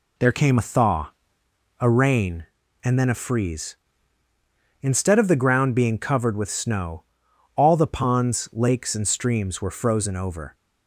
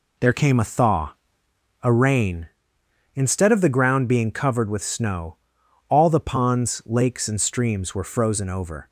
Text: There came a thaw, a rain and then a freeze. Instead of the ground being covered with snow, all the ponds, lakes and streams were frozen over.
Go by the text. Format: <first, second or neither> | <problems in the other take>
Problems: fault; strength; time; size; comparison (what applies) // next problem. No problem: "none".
first | skips "and then a freeze"; at 2.8 s